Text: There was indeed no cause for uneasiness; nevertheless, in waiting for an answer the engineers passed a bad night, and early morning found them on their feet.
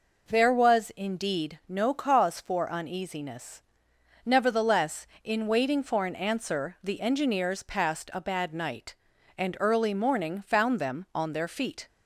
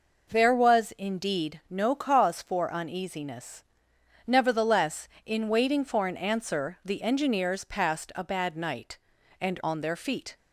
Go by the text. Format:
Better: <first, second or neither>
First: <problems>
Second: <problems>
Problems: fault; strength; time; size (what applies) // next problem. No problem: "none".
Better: first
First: none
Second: skips "early morning found them"; at 9.6 s